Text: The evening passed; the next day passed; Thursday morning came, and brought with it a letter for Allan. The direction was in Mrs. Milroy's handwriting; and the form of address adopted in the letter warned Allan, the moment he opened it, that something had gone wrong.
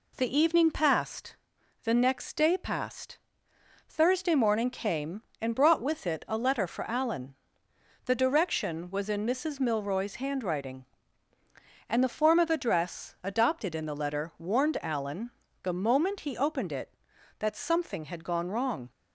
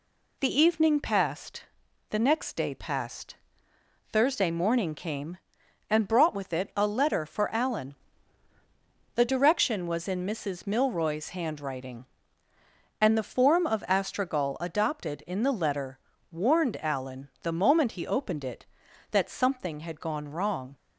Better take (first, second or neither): first